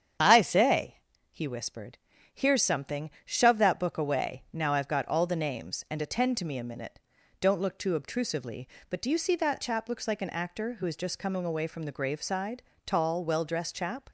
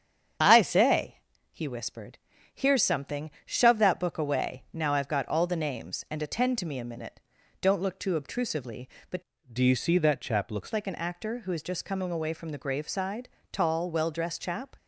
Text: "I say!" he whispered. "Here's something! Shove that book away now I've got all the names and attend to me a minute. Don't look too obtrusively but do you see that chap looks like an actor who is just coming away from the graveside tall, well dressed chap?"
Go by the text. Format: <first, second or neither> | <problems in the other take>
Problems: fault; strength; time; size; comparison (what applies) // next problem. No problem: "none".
first | starts louder than the rest; strong; until 1.7 s; 8 dB; strong in the first // changes voice from "do" to "looks"; from 9.5 to 10.7 s; 1.2 s long // pauses between "graveside" and "tall"; slight; at 13.2 s; 0.24 s long; slight in the first